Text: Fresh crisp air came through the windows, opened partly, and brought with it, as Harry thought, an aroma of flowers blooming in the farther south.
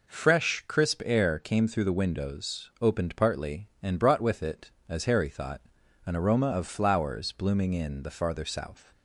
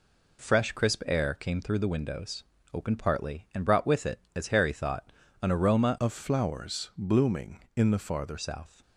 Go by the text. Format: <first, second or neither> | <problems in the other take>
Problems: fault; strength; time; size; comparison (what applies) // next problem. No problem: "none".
first | changes voice from "of" to "farther"; from 6.0 to 8.3 s; 2.3 s long